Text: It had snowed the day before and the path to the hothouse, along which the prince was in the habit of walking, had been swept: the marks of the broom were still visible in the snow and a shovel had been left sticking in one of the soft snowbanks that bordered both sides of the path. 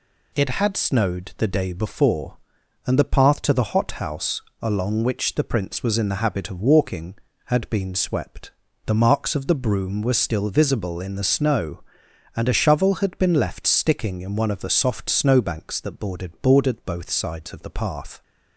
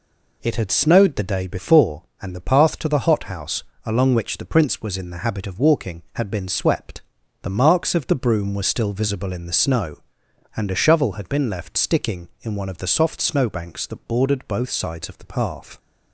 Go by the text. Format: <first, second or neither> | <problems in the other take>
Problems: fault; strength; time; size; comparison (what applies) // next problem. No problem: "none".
second | says "bordered" twice; at 16.4 s